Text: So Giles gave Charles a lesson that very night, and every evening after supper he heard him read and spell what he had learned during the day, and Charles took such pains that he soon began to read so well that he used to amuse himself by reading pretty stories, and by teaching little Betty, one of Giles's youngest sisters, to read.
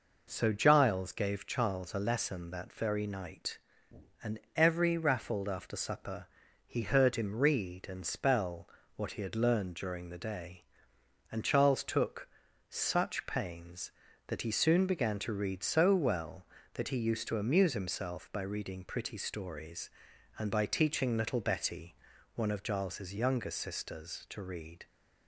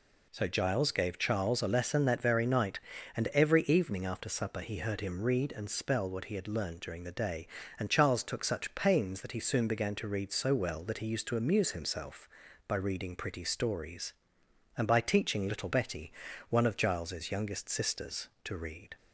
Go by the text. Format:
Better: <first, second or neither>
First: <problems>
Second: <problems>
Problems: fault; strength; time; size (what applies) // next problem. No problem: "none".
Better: second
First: pauses between "and" and "every"; slight; at 4.3 s; 0.16 s long // says "raffled" for "evening"; at 4.9 s // pauses between "supper" and "he"; at 6.2 s; 0.40 s long // pauses between "spell" and "what"; slight; at 8.6 s; 0.26 s long // pauses between "took" and "such"; at 12.2 s; 0.40 s long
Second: none